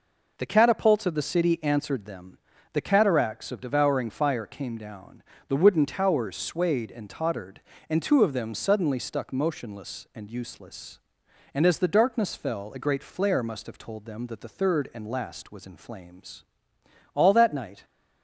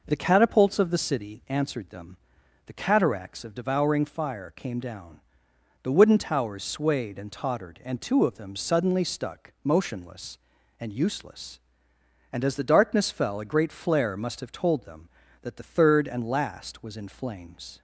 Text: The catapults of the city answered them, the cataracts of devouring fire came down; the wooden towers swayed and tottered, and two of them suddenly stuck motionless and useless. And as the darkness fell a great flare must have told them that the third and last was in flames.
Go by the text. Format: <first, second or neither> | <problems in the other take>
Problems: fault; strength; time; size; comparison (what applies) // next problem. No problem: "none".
second | goes on to say "All that night"; noticeable; from 17.1 s on; 0.70 s long